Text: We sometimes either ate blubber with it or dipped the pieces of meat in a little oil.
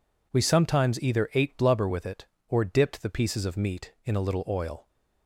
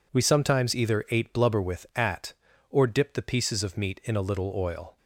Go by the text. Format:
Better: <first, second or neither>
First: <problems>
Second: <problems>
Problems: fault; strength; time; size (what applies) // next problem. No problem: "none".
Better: first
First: none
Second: says "at" for "it"; at 1.9 s